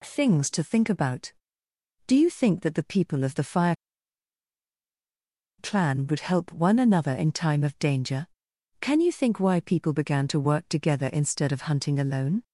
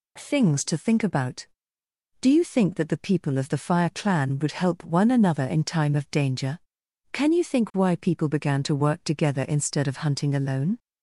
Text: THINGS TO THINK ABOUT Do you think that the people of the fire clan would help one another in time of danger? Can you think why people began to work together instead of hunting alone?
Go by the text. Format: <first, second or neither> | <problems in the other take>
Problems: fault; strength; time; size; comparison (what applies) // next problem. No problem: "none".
second | pauses between "fire" and "clan"; strong; at 3.7 s; 1.8 s long